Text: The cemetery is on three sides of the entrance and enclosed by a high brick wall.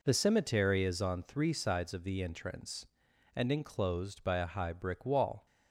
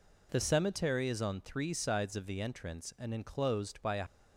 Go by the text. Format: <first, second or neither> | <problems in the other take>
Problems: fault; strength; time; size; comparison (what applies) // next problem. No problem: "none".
first | stops before "high brick wall"; at 4.0 s